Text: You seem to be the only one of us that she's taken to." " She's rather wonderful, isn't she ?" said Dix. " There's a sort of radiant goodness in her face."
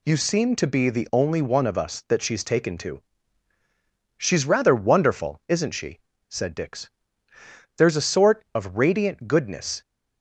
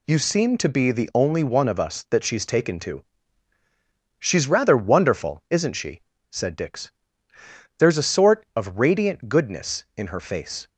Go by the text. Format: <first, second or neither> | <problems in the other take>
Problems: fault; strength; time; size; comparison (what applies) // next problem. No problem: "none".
second | stops before "in her face"; at 9.8 s